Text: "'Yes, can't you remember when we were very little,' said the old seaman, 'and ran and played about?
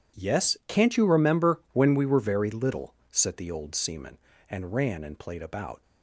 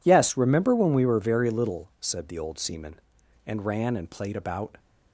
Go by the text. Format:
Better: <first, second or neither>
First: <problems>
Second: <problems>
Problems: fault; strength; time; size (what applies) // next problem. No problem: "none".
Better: first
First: none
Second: skips "can't you"; at 0.3 s